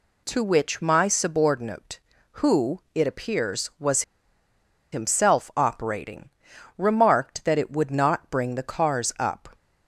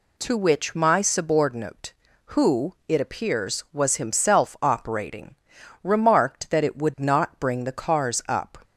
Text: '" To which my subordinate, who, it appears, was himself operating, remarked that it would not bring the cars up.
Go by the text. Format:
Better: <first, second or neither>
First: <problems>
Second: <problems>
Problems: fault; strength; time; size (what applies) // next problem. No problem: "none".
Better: second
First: pauses between "was" and "himself"; noticeable; at 4.0 s; 0.90 s long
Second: none